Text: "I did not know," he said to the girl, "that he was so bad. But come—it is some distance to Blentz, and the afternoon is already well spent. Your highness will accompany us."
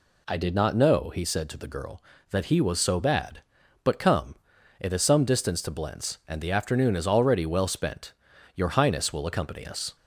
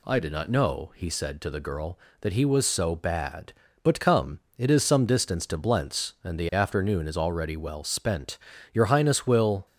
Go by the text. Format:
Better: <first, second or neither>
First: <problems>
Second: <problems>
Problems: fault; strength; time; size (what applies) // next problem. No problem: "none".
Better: first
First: none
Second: stops before "accompany us"; at 9.6 s